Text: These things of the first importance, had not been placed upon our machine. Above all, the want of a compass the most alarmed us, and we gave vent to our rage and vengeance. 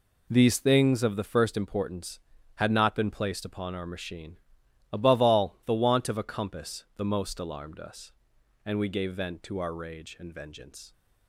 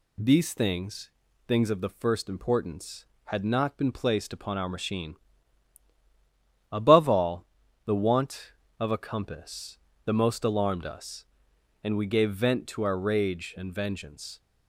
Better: first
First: none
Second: says "things" twice; at 1.4 s // pauses between "compass" and "the"; slight; at 9.7 s; 0.26 s long

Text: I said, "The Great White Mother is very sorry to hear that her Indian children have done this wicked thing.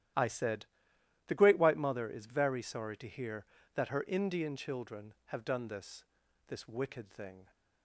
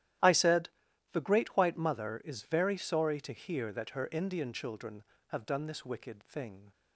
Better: second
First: starts louder than the rest; strong; until 1.7 s; 12.5 dB // says "this" twice; at 6.4 s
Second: starts louder than the rest; strong; until 1.6 s; 13 dB

